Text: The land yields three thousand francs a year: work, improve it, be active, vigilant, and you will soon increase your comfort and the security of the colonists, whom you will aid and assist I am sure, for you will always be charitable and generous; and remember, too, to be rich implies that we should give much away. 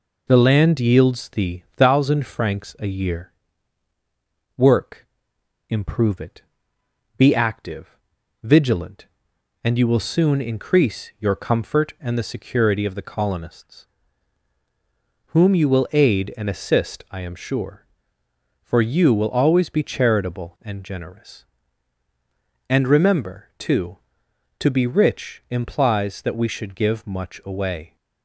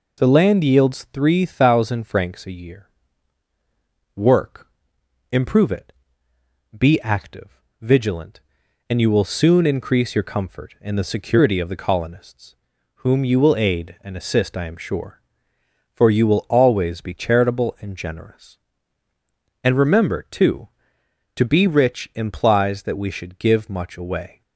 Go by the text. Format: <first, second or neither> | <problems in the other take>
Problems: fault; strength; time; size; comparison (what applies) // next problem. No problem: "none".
second | says "thee" for "three"; at 1.2 s